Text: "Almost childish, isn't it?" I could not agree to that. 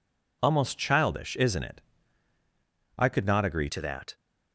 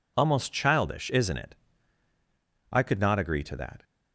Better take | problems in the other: second | changes voice at "to"; from 3.6 s on; 0.5 s long

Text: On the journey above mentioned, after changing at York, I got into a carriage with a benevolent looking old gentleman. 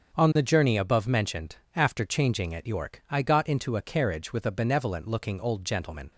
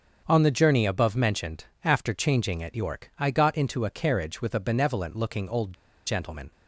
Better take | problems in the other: first | starts louder than the rest; until 1.2 s; 7 dB; also in the first // pauses between "old" and "gentleman"; slight; at 5.7 s; 0.33 s long

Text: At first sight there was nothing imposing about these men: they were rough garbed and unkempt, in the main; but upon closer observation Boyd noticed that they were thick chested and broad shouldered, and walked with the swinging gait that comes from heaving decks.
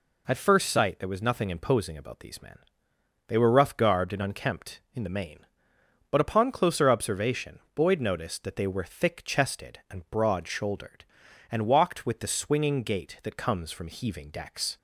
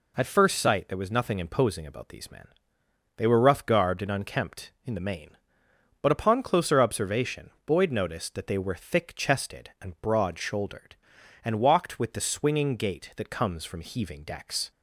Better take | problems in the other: neither | pauses between "observation" and "Boyd"; slight; the same in both

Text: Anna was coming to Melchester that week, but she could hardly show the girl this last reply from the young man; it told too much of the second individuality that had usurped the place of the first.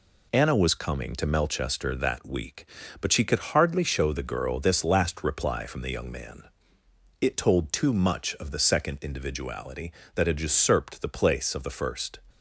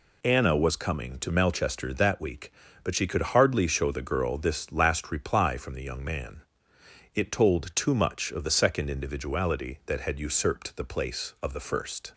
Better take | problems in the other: neither | none

